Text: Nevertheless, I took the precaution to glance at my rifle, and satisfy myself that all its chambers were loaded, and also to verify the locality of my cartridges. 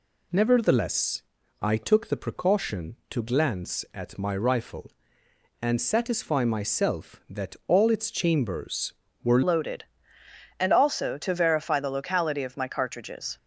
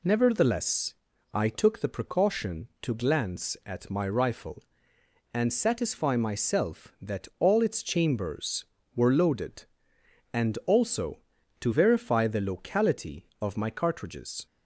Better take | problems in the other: second | changes voice at "loaded"; from 9.4 s on; 3.9 s long

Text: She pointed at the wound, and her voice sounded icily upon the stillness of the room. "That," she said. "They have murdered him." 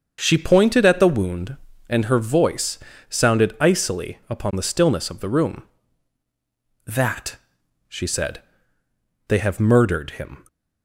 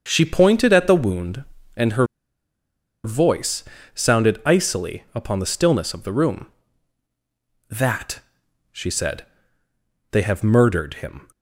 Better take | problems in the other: first | starts louder than the rest; until 1.0 s; 7 dB; also in the first // pauses between "her" and "voice"; at 2.0 s; 0.98 s long // pauses between "voice" and "sounded"; slight; at 3.6 s; 0.30 s long; slight in the first

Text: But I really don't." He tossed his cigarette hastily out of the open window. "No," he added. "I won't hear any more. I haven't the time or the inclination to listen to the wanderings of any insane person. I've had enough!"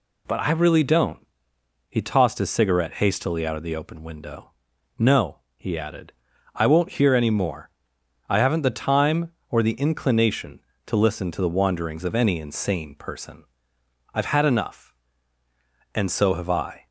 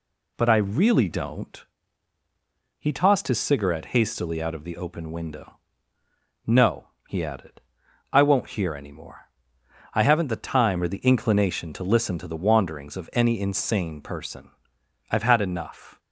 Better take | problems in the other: second | goes on to say "And so have I"; noticeable; from 15.9 s on; 0.92 s long

